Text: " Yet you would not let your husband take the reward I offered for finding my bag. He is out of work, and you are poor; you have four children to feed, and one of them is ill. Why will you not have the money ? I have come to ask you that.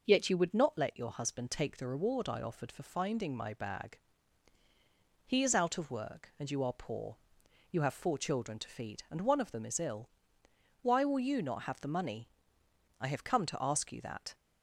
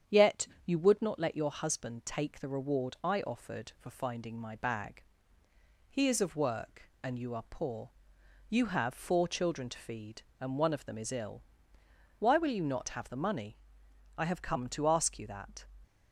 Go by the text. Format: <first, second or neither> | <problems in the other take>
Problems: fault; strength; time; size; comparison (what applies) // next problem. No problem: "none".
first | starts louder than the rest; strong; until 1.2 s; 8 dB // pauses between "Yet" and "you"; slight; at 0.4 s; 0.18 s long // skips "out"; at 6.2 s